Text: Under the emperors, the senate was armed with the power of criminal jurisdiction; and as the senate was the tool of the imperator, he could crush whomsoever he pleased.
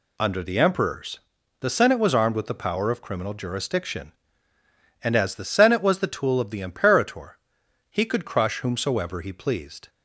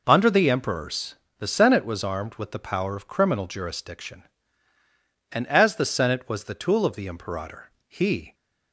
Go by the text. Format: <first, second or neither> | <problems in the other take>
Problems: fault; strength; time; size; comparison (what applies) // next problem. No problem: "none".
first | stops before "could crush whomsoever he pleased"; at 8.3 s